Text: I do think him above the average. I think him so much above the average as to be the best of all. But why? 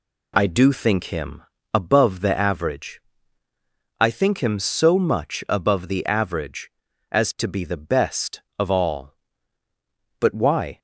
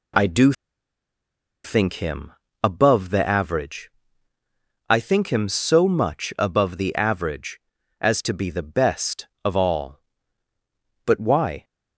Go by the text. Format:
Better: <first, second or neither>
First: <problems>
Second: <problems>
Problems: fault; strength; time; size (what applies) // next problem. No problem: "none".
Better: first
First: pauses between "him" and "above"; slight; at 1.4 s; 0.30 s long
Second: pauses between "do" and "think"; at 0.5 s; 1.1 s long // pauses between "him" and "above"; slight; at 2.3 s; 0.30 s long